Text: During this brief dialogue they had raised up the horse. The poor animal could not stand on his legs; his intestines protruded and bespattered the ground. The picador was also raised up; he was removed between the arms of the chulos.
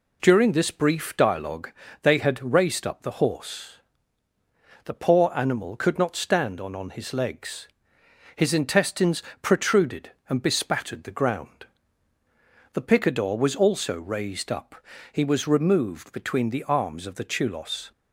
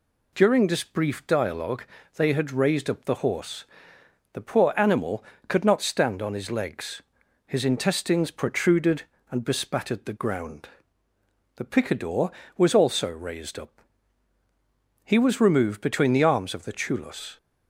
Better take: second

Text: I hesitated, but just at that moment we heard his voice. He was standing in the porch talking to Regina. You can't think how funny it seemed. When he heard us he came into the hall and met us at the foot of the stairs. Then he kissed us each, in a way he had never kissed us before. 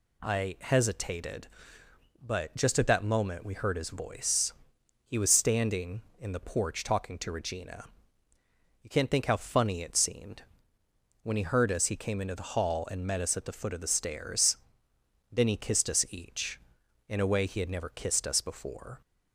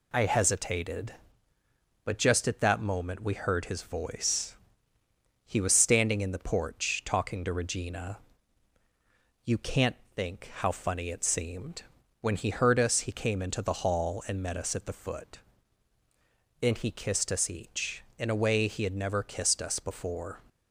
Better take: first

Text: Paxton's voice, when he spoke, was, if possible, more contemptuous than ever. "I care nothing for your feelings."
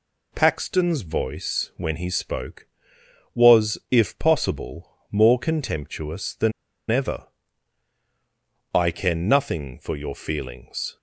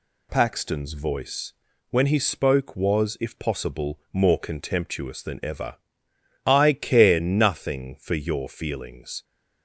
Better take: second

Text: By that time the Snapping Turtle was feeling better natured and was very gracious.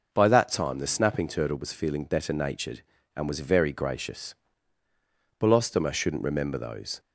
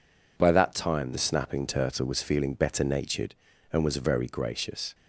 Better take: second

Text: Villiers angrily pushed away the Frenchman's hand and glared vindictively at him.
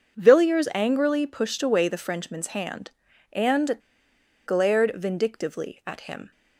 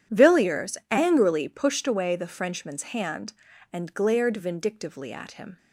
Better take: second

